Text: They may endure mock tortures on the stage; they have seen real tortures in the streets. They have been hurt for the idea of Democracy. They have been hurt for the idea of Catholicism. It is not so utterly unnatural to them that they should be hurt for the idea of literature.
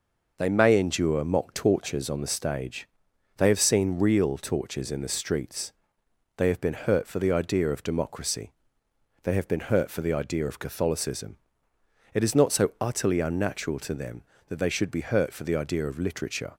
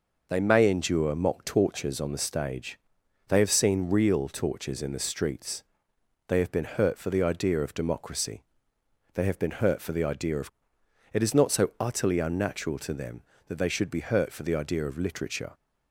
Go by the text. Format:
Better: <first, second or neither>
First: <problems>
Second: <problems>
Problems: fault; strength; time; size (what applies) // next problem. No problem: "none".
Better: first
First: none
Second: skips "Catholicism"; at 10.8 s